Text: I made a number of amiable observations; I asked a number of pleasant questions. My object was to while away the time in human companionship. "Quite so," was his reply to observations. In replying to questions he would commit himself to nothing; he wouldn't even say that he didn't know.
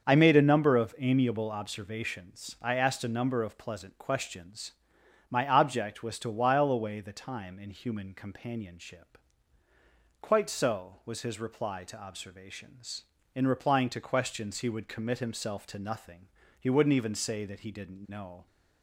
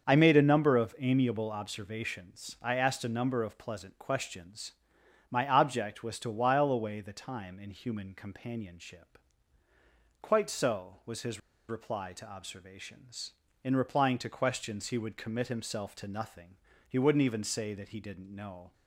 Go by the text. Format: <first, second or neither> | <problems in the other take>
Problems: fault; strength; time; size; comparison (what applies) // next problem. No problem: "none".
first | starts louder than the rest; until 1.1 s; 7 dB; also in the first // pauses between "his" and "reply"; slight; at 11.3 s; 0.29 s long